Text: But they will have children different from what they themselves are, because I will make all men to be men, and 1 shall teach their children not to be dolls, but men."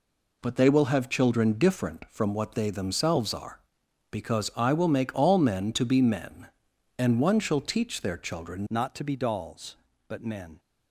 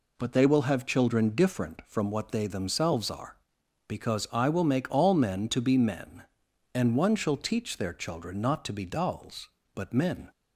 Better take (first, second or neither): second